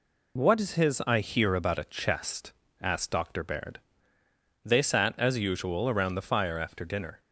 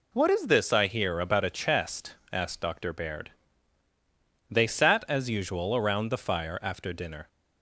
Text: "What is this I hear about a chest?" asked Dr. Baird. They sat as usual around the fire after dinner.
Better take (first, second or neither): second